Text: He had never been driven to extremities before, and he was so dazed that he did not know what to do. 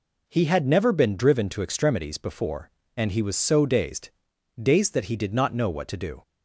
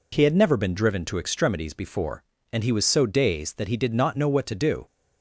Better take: second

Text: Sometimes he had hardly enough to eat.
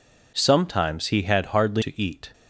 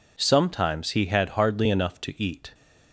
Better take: second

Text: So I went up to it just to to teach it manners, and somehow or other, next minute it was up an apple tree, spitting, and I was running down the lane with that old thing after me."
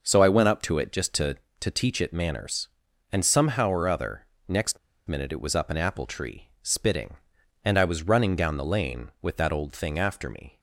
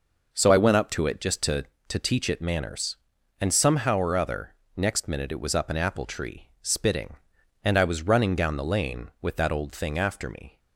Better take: second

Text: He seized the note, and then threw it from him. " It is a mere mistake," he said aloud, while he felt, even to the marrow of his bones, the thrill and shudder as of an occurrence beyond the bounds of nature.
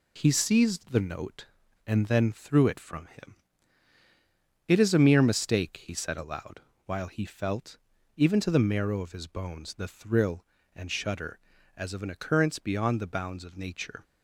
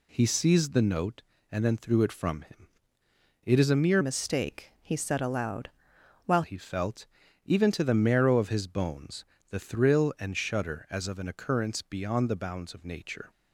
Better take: first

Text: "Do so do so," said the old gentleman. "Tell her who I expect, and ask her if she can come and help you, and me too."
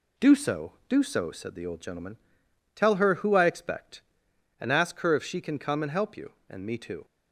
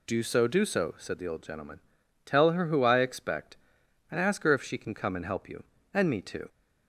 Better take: neither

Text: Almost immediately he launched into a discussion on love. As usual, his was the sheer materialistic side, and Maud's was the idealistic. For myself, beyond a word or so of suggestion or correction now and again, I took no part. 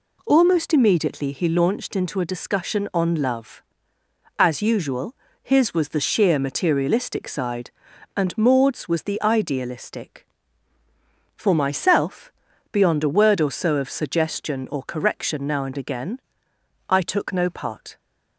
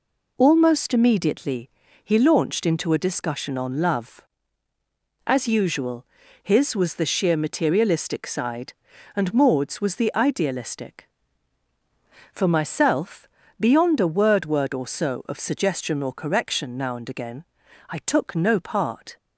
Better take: first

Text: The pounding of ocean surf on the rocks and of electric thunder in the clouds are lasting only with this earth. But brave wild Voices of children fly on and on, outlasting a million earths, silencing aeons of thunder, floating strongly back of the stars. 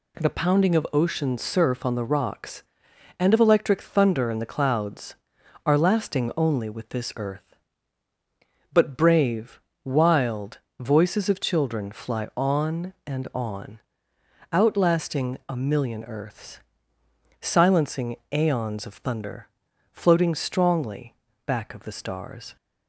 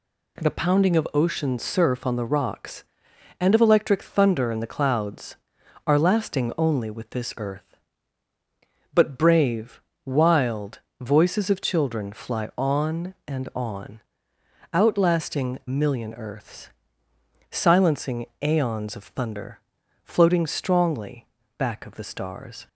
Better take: first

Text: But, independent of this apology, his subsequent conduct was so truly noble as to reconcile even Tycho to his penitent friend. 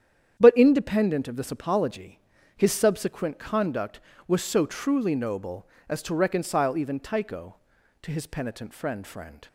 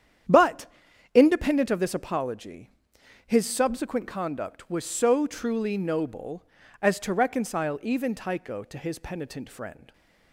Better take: second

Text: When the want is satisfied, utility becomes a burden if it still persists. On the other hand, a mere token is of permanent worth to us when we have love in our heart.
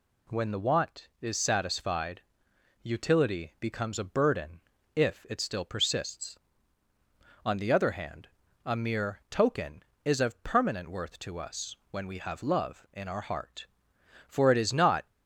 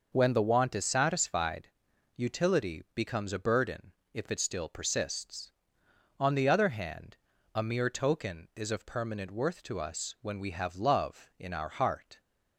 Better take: second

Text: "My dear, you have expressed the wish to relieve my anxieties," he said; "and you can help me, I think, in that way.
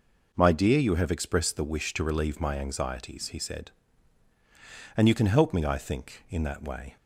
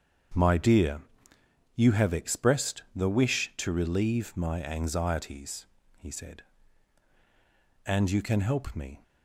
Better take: first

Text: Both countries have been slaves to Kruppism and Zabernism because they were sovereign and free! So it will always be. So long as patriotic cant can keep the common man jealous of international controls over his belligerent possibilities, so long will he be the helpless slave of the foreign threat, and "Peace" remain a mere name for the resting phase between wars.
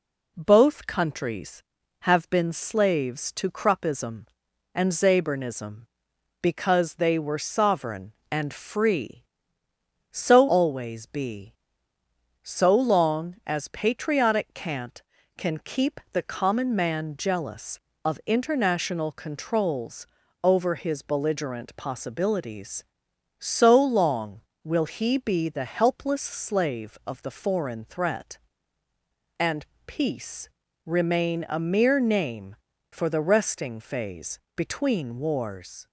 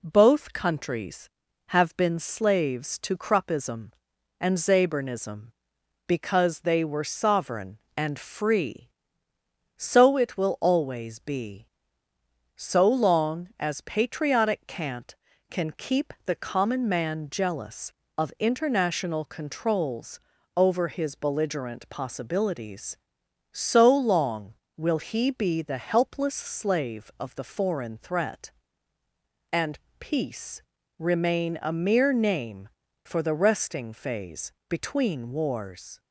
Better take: second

